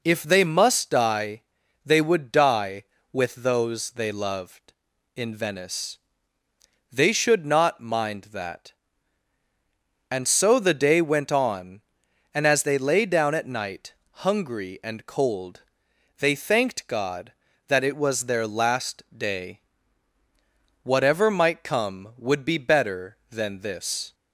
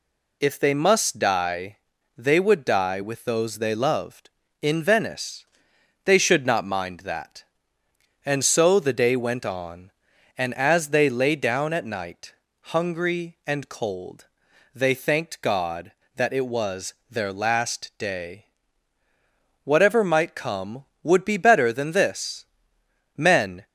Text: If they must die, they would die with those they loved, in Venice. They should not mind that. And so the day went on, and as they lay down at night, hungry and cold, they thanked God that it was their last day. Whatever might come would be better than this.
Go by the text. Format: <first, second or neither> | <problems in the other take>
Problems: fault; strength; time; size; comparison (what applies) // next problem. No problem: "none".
first | pauses between "was" and "their"; slight; at 16.9 s; 0.16 s long // goes on to say "Men"; slight; from 23.1 s on; 0.48 s long